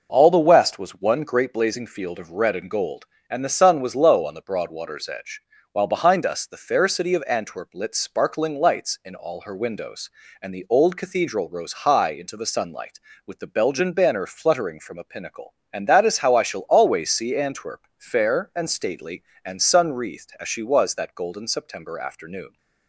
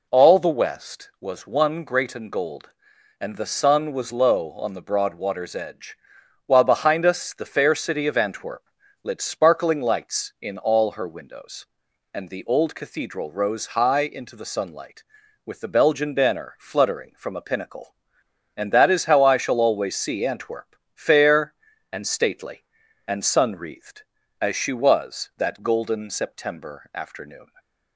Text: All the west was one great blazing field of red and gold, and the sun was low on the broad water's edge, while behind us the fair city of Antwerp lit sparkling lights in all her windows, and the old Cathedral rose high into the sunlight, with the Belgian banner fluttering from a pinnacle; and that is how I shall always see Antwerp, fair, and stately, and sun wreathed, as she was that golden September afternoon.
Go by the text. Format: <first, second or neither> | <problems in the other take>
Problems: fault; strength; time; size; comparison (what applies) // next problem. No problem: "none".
first | skips "blazing field of red"; at 2.1 s // pauses between "Antwerp" and "lit"; at 8.6 s; 0.40 s long